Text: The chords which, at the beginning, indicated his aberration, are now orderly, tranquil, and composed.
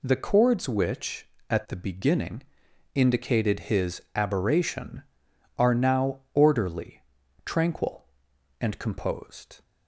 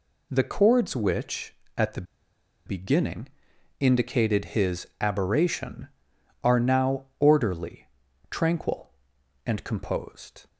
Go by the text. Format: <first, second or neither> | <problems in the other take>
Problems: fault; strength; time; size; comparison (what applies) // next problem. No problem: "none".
first | pauses between "the" and "beginning"; noticeable; at 2.0 s; 0.63 s long